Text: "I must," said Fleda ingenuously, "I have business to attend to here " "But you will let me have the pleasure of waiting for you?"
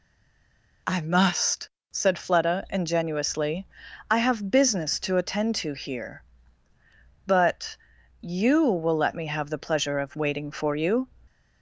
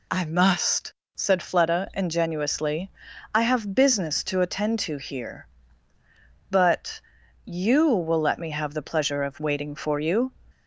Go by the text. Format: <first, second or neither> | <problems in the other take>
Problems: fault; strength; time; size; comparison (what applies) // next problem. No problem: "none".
second | stays silent before the first word; slight; until 0.8 s; 0.8 s long // pauses between "But" and "you"; at 7.7 s; 0.42 s long; also in the second